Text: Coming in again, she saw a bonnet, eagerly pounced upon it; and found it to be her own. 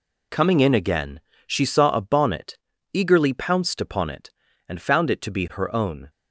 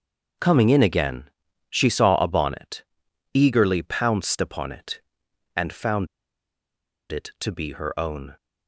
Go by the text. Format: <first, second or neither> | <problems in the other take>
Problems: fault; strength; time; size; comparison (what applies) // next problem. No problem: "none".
first | starts louder than the rest; until 1.8 s; 6.5 dB // pauses between "found" and "it"; at 6.0 s; 1.0 s long